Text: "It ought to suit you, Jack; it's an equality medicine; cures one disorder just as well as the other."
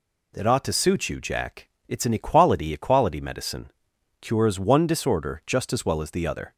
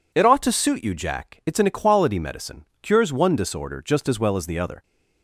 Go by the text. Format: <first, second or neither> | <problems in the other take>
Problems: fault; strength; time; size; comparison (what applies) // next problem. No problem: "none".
second | says "equality" twice; at 2.7 s